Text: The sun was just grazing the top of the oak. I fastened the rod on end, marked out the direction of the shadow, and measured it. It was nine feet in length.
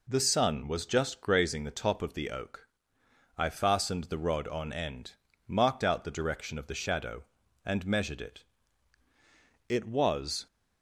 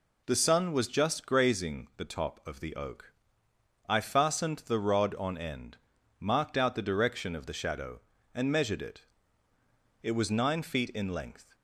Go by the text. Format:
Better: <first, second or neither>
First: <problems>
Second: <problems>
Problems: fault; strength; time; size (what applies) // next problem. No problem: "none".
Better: second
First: stops before "nine feet in length"; at 10.4 s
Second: none